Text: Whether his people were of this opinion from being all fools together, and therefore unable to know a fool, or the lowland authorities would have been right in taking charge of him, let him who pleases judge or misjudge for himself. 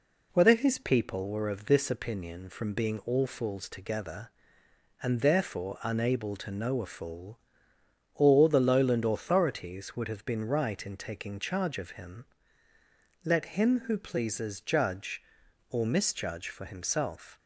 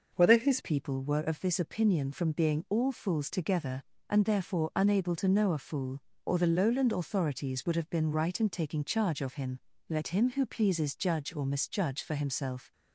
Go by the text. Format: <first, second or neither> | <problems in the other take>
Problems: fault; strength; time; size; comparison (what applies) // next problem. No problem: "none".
first | changes voice at "people"; from 0.6 s on; 12.1 s long